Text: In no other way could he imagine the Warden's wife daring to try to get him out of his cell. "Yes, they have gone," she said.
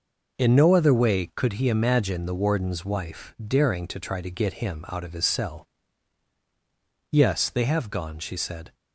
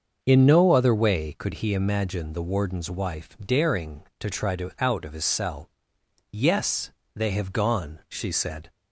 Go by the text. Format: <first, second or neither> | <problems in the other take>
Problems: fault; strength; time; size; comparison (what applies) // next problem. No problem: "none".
first | starts louder than the rest; until 1.2 s; 6.5 dB // skips "get him"; at 4.7 s